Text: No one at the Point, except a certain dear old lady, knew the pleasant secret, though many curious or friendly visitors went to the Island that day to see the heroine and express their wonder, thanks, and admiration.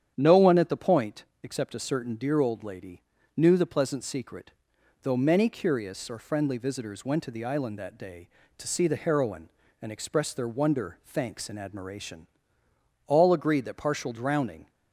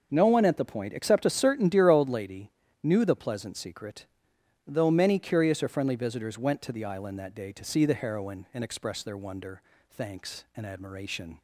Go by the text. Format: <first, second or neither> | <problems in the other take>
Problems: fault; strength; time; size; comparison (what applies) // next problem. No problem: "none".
second | starts louder than the rest; strong; until 1.1 s; 9 dB; noticeable in the second // goes on to say "All agreed that partial drowning"; from 13.0 s on; 1.6 s long